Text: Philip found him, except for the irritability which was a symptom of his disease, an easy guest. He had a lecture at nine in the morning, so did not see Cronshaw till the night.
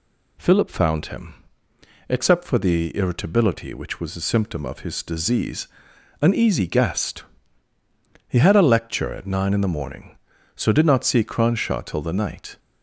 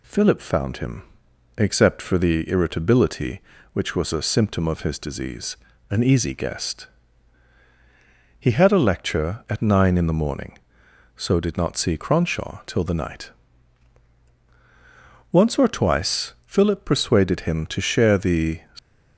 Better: first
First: none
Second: goes on to say "Once or twice Philip persuaded him to share the"; strong; from 15.3 s on; 3.2 s long

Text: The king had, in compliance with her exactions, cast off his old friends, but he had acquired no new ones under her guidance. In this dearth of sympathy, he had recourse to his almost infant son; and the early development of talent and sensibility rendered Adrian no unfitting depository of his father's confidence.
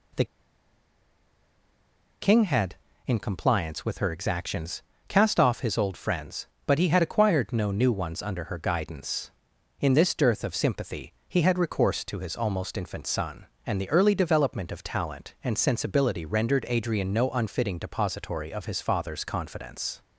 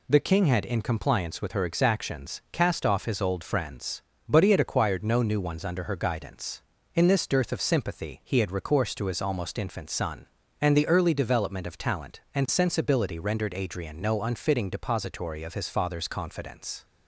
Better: second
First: pauses between "The" and "king"; strong; at 0.2 s; 1.9 s long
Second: none

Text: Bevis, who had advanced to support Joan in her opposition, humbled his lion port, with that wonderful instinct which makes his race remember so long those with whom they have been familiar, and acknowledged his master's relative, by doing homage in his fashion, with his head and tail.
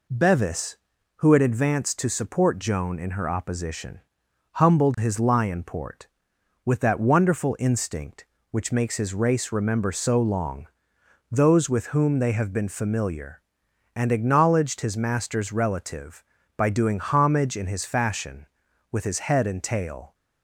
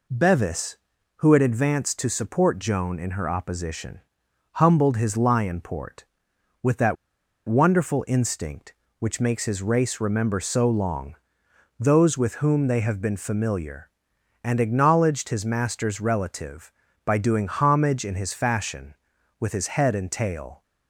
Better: first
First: pauses between "long" and "those"; noticeable; at 10.6 s; 0.64 s long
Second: pauses between "that" and "wonderful"; noticeable; at 6.9 s; 0.51 s long // pauses between "long" and "those"; noticeable; at 11.1 s; 0.64 s long

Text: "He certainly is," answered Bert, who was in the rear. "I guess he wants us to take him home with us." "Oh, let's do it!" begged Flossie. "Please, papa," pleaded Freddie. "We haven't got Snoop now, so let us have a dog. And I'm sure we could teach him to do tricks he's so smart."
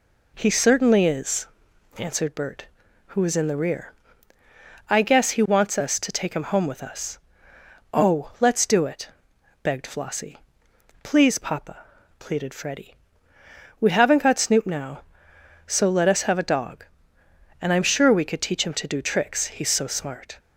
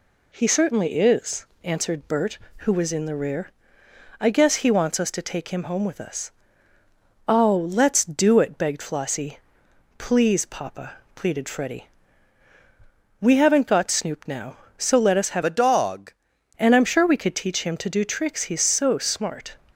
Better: first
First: none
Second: changes voice from "a" to "dog"; from 15.4 to 16.1 s; 0.7 s long

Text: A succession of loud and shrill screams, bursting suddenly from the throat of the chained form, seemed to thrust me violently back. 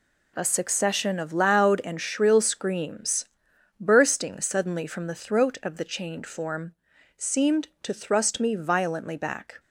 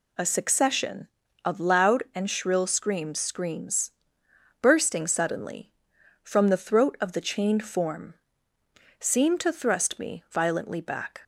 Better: first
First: none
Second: says "screams" twice; at 3.1 s

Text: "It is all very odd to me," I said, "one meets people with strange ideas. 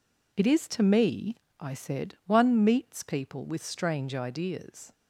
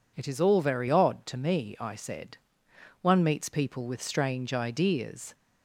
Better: second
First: skips "all very odd"; at 0.6 s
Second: none

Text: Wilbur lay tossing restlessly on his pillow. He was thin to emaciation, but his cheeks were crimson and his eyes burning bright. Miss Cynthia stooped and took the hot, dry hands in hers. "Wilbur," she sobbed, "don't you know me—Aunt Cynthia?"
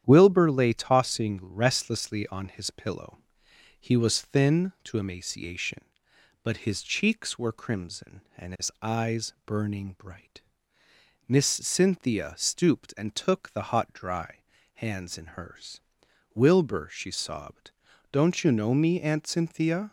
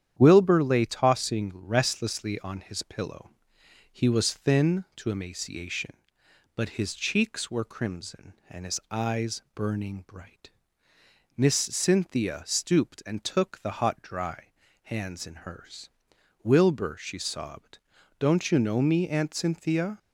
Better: neither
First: starts louder than the rest; strong; until 1.0 s; 9.5 dB // pauses between "dry" and "hands"; at 14.3 s; 0.40 s long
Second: starts louder than the rest; strong; until 1.2 s; 9.5 dB // pauses between "dry" and "hands"; at 14.4 s; 0.40 s long

